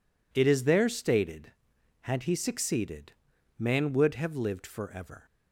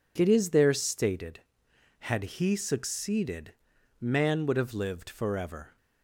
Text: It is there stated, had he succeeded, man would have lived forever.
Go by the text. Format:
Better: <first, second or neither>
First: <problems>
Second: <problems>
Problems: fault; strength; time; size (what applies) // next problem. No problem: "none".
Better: neither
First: none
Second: none